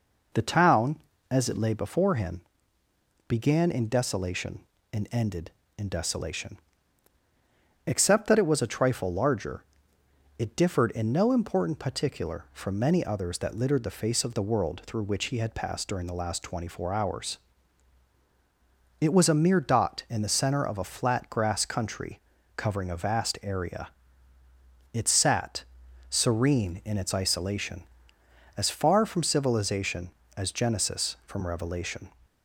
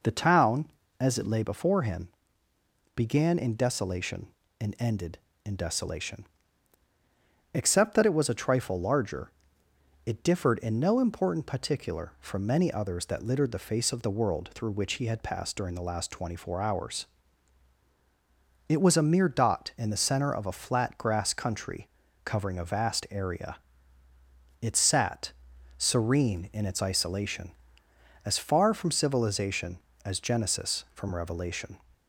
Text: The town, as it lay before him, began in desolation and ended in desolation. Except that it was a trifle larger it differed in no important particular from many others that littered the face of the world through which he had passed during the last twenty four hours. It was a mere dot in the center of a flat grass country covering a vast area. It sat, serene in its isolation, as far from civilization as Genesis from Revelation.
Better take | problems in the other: neither | pauses between "larger" and "it"; noticeable; the same in both // pauses between "country" and "covering"; the same in both

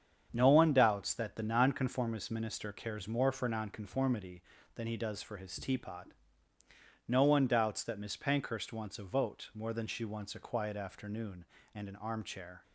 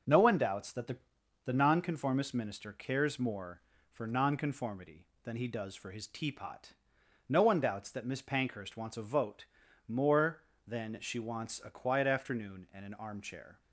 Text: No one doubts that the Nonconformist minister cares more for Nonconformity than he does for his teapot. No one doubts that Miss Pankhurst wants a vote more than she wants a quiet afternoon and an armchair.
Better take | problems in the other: first | starts louder than the rest; until 1.5 s; 6.5 dB; strong in the first // says "the" twice; at 1.4 s // pauses between "vote" and "more"; at 9.4 s; 0.42 s long

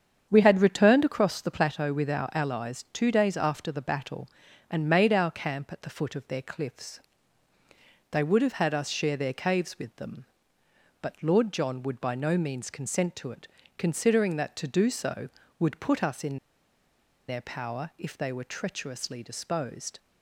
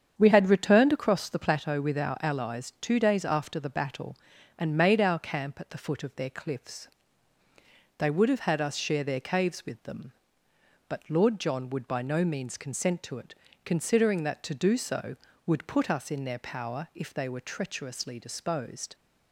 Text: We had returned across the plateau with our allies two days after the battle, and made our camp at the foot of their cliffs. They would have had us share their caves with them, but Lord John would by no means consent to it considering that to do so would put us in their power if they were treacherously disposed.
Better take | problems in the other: second | starts louder than the rest; strong; until 1.3 s; 8 dB; strong in the second // pauses between "it" and "considering"; slight; at 13.4 s; 0.32 s long; slight in the second // pauses between "in" and "their"; noticeable; at 16.3 s; 0.92 s long

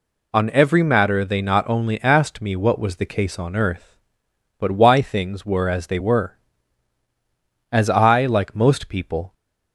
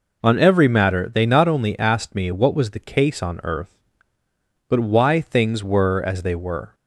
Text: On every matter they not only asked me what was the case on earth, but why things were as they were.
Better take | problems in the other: second | goes on to say "As I like most people"; from 7.7 s on; 1.6 s long

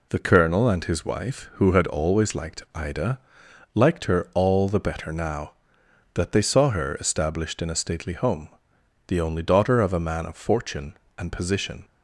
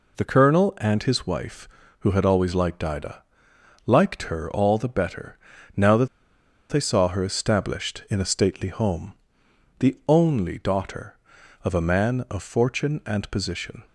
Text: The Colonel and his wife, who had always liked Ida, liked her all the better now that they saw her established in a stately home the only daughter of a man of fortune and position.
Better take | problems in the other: first | pauses between "better" and "now"; at 5.3 s; 0.38 s long // pauses between "that" and "they"; noticeable; at 6.0 s; 0.61 s long // pauses between "home" and "the"; noticeable; at 9.1 s; 0.68 s long; noticeable in the first

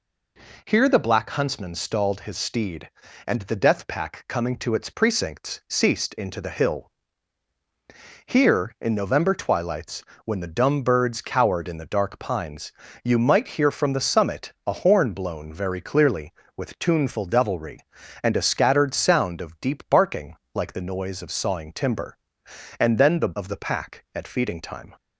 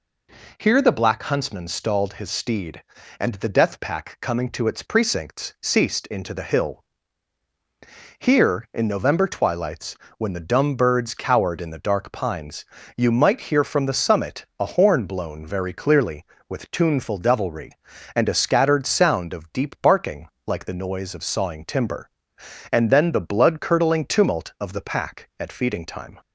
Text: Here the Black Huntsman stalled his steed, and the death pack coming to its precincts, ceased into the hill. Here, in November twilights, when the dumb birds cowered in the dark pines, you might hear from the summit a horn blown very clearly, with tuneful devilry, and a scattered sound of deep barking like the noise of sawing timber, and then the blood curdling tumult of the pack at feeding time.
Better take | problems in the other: second | pauses between "barking" and "like"; slight; at 20.3 s; 0.16 s long; slight in the second // skips "blood curdling tumult"; at 23.3 s

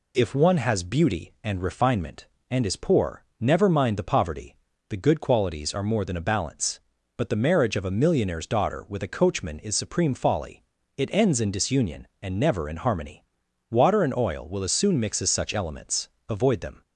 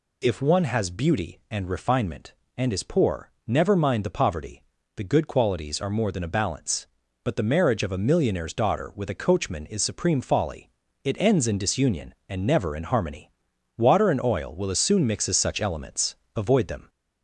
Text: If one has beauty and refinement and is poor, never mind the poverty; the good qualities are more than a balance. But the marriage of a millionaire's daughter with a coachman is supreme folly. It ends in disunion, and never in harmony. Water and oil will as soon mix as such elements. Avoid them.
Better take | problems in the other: first | gets louder; slight; throughout; 2.5 dB

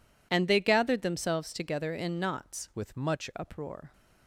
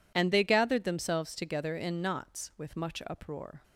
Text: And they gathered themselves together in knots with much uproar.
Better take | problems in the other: second | changes voice from "with" to "much"; from 2.7 to 3.3 s; 0.6 s long

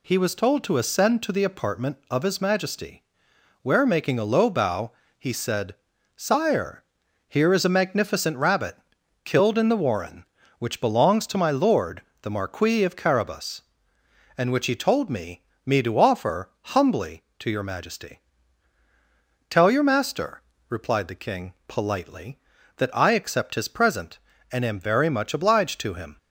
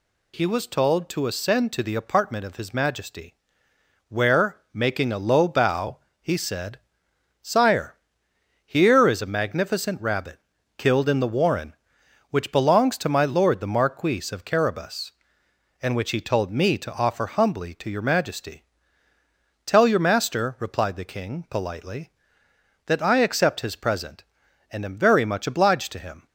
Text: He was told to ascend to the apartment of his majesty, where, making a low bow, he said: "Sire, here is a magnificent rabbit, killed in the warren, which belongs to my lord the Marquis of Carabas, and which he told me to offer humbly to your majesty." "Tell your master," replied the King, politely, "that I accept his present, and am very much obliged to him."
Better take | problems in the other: second | pauses between "lord" and "the"; slight; at 12.0 s; 0.18 s long // says "me" twice; at 15.6 s // pauses between "offer" and "humbly"; slight; at 16.5 s; 0.24 s long

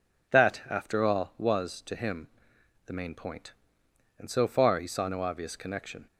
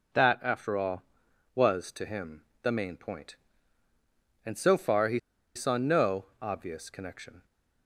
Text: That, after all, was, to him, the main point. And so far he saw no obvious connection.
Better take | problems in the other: first | pauses between "he" and "saw"; slight; at 5.1 s; 0.35 s long // pauses between "no" and "obvious"; slight; at 6.2 s; 0.16 s long

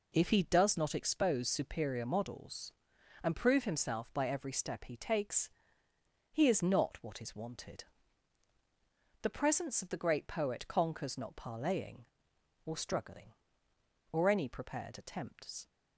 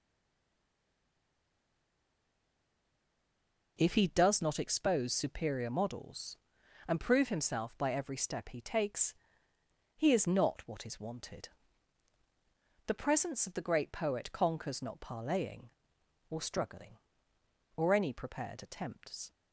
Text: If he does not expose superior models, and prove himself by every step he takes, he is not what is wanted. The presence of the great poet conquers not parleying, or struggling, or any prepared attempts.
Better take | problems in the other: first | stays silent before the first word; strong; until 3.7 s; 3.7 s long

